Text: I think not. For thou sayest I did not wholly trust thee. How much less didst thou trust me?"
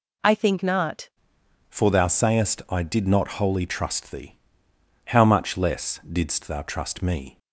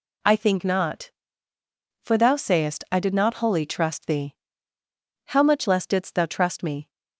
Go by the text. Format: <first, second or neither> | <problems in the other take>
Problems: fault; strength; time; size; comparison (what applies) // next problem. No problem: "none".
second | changes voice at "For"; from 1.7 s on; 5.6 s long